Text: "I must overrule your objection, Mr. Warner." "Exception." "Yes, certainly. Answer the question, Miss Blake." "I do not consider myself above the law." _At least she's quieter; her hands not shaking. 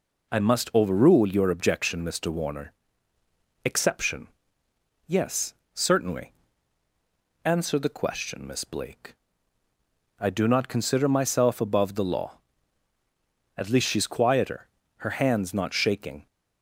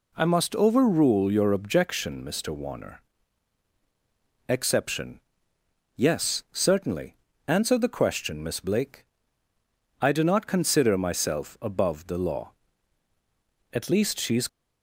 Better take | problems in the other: first | stops before "quieter her hands not shaking"; at 14.4 s

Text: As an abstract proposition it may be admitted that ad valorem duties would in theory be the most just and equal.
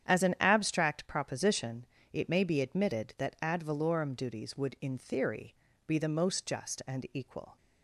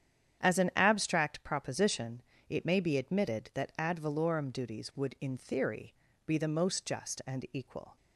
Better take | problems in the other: neither | starts louder than the rest; strong; the same in both // pauses between "proposition" and "it"; slight; the same in both // pauses between "theory" and "be"; slight; the same in both

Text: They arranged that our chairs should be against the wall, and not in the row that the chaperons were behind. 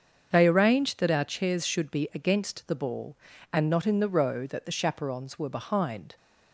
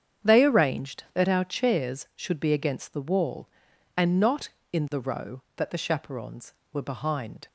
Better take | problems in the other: second | starts louder than the rest; until 1.3 s; 7 dB; strong in the second // says "ball" for "wall"; at 2.7 s

